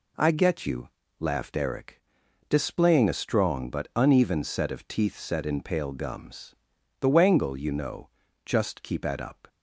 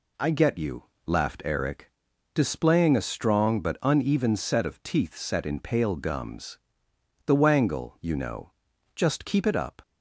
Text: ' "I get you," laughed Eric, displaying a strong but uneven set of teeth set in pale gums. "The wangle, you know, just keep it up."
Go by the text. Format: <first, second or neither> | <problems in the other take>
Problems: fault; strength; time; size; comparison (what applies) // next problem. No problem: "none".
second | says "at" for "it"; at 9.0 s